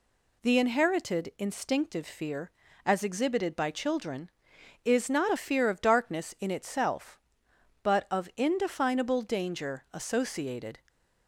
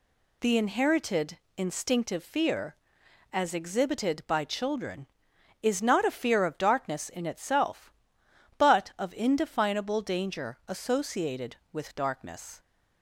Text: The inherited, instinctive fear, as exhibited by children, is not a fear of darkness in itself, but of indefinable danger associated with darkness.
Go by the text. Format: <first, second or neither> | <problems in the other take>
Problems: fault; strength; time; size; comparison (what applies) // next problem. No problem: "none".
second | stops before "with darkness"; at 10.8 s